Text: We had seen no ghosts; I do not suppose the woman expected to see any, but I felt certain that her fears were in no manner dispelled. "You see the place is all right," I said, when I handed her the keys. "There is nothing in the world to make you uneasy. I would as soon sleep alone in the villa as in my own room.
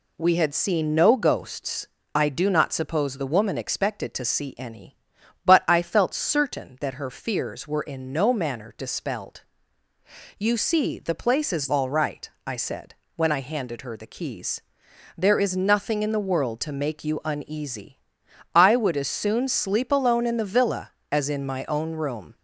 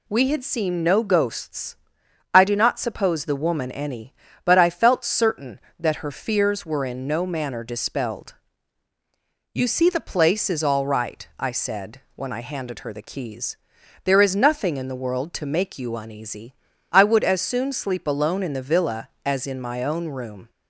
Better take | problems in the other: first | skips "expected to see"; at 3.7 s

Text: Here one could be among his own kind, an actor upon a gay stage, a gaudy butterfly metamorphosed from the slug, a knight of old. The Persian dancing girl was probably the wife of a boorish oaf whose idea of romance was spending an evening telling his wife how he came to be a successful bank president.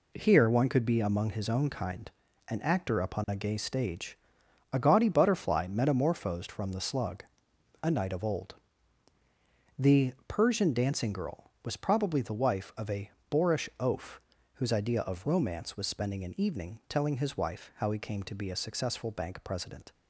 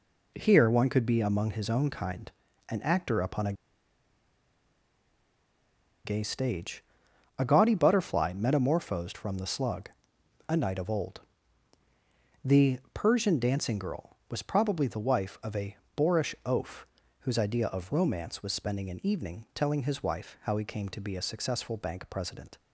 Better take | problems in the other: first | pauses between "a" and "gay"; strong; at 3.5 s; 2.5 s long // pauses between "The" and "Persian"; slight; at 12.7 s; 0.16 s long; slight in the first // pauses between "a" and "boorish"; slight; at 15.7 s; 0.20 s long; slight in the first // pauses between "oaf" and "whose"; slight; at 16.8 s; 0.36 s long; slight in the first

